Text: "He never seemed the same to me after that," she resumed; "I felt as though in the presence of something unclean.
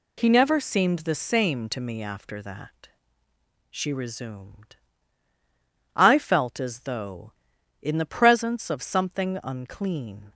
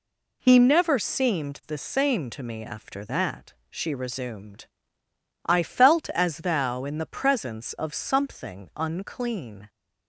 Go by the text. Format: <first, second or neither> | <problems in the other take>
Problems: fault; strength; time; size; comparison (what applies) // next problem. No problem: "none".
first | says "thou" for "though"; at 6.3 s